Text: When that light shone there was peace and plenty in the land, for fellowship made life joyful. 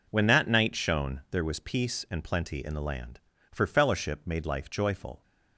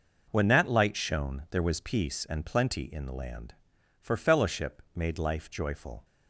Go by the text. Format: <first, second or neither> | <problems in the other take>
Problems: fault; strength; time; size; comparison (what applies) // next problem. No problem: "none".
second | says "night" for "light"; at 0.4 s